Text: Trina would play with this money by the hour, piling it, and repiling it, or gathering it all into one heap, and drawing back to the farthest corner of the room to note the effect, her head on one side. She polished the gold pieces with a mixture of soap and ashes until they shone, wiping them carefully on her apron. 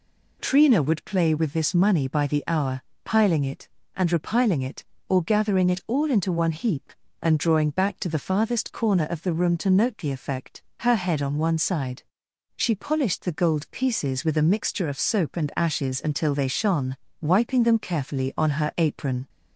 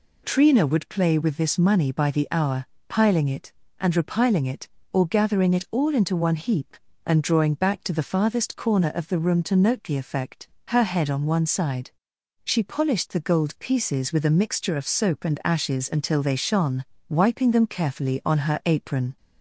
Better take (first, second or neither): neither